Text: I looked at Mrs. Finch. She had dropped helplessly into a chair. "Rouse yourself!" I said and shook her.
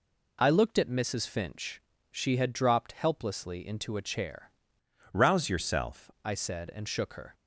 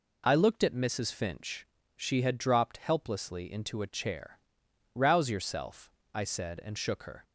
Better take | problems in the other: second | changes voice from "Rouse" to "yourself"; from 5.1 to 6.0 s; 0.9 s long

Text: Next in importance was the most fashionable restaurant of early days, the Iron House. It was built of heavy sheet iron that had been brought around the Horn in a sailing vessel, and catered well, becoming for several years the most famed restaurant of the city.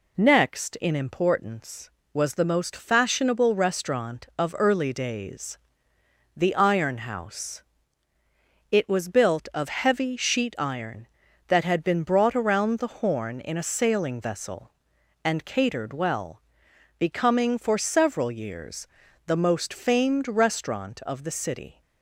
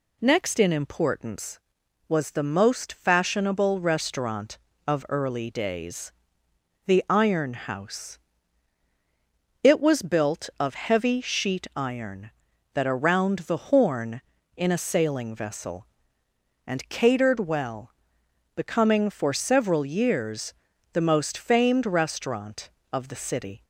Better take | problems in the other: first | skips "had been brought"; at 12.8 s // pauses between "years" and "the"; at 20.5 s; 0.40 s long; also in the first

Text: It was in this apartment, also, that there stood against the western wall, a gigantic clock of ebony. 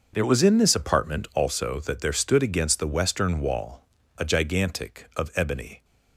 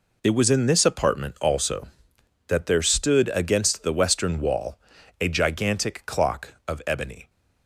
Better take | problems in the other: second | starts louder than the rest; until 1.1 s; 6 dB // skips "clock"; at 5.1 s

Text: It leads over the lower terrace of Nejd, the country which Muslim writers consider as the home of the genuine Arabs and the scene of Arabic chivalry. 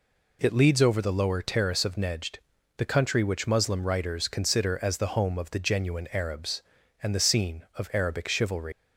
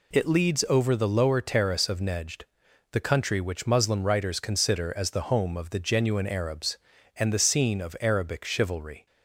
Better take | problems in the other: second | leaves "chivalry" unfinished; at 8.7 s; 140 ms

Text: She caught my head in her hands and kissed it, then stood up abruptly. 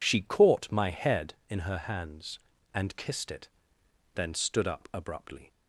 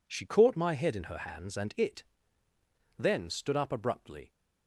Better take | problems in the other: first | skips "kissed"; at 1.7 s

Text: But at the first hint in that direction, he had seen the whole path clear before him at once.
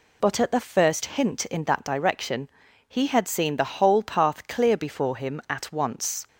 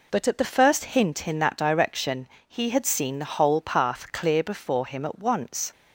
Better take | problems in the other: neither | none

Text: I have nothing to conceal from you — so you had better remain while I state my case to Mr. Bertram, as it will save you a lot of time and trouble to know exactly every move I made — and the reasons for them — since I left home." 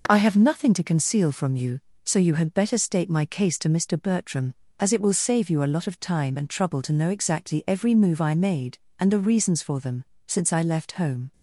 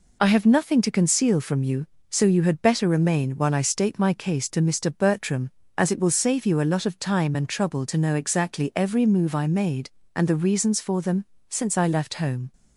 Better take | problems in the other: second | skips "remain while I"; at 2.7 s

